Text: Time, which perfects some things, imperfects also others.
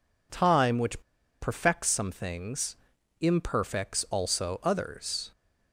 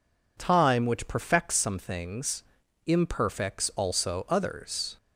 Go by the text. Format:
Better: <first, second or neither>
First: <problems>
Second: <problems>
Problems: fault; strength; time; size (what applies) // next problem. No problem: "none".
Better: second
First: pauses between "which" and "perfects"; at 1.0 s; 0.40 s long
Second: none